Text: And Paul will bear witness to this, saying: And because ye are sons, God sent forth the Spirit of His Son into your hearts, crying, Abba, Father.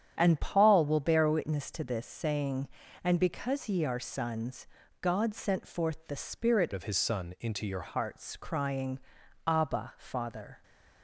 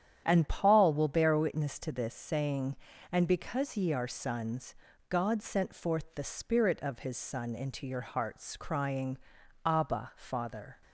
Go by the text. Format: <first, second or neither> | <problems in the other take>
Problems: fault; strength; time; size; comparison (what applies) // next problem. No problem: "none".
second | starts louder than the rest; strong; until 1.1 s; 9 dB; strong in the second // changes voice from "of" to "your"; from 6.7 to 7.8 s; 1.1 s long